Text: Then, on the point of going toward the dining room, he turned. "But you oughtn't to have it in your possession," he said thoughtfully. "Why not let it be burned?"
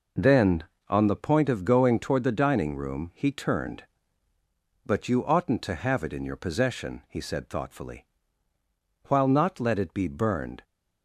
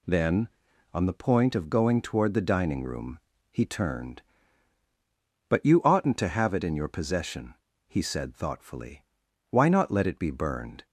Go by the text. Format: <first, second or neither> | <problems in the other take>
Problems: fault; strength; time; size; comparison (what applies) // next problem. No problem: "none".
second | says "While" for "Why"; at 9.0 s